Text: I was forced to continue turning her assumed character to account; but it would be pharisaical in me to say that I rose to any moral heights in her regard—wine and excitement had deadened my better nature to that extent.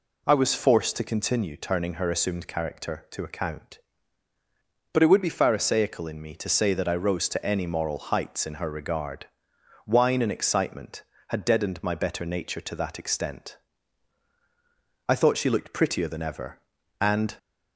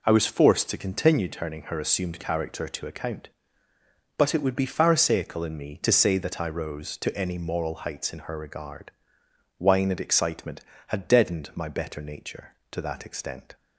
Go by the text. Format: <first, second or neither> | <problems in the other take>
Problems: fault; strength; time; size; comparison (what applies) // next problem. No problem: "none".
second | goes on to say "I thought she looked prettier than ever and"; strong; from 15.0 s on; 2.2 s long